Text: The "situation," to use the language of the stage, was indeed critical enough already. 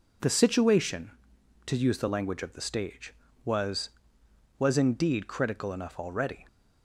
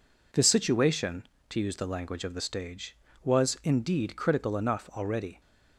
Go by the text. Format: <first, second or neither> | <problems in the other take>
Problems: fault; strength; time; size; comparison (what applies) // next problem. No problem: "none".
second | says "was" twice; at 4.5 s